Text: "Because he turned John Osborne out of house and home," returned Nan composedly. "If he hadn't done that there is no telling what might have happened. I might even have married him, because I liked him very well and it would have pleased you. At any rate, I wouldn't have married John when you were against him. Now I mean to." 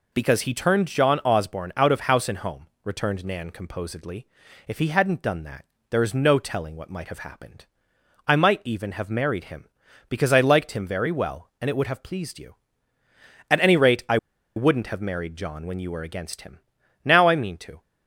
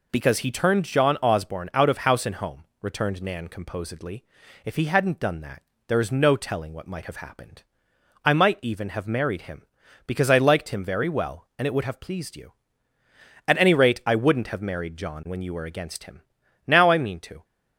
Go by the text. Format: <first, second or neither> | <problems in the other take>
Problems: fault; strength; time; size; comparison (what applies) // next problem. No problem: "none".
second | pauses between "that" and "there"; slight; at 5.6 s; 0.24 s long; slight in the second // pauses between "I" and "wouldn't"; at 14.1 s; 0.39 s long